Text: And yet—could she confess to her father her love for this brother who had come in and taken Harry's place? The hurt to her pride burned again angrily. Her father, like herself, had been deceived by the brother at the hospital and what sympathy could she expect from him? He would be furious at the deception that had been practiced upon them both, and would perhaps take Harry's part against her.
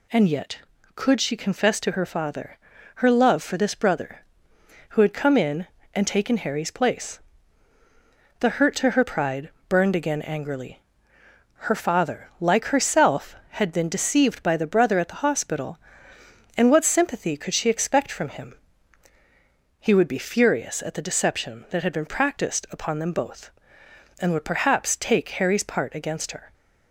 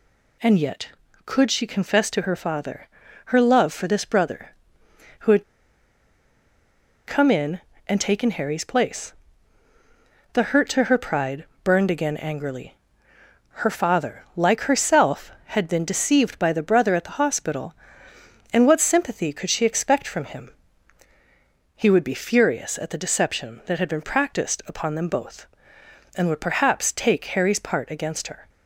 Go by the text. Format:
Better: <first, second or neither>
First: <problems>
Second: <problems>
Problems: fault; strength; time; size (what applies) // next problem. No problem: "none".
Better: first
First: pauses between "father" and "her"; at 2.5 s; 0.38 s long // pauses between "pride" and "burned"; slight; at 9.4 s; 0.18 s long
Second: pauses between "father" and "her"; at 2.8 s; 0.38 s long // pauses between "had" and "come"; strong; at 5.4 s; 1.6 s long // pauses between "pride" and "burned"; slight; at 11.4 s; 0.18 s long